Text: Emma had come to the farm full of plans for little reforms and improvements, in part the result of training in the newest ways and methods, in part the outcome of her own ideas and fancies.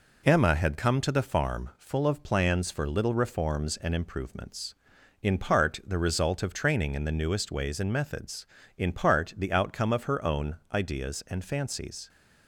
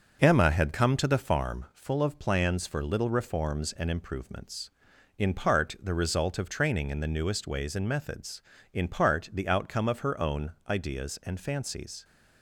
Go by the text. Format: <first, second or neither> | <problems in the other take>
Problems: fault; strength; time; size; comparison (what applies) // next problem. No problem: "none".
first | starts louder than the rest; noticeable; until 1.5 s; 6 dB // pauses between "own" and "ideas"; slight; at 10.5 s; 0.16 s long; slight in the first